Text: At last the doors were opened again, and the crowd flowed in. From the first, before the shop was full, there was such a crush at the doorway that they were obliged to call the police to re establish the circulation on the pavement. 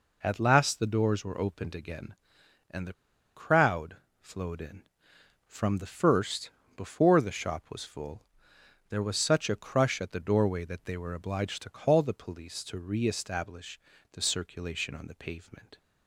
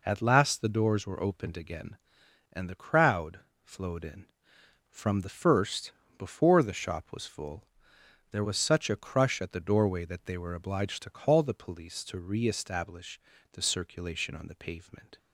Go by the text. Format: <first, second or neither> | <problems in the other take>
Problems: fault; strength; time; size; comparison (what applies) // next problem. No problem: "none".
second | pauses between "the" and "crowd"; at 2.9 s; 0.42 s long // pauses between "crowd" and "flowed"; slight; at 3.9 s; 0.22 s long; slight in the second // pauses between "establish" and "the"; slight; at 13.7 s; 0.32 s long; slight in the second